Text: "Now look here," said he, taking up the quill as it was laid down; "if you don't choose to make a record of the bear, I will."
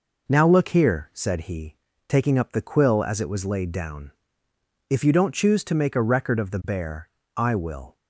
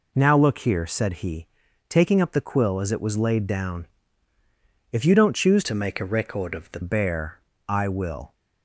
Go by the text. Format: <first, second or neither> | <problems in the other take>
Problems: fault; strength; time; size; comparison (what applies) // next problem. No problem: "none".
first | changes voice from "to" to "the"; from 5.6 to 6.7 s; 1.1 s long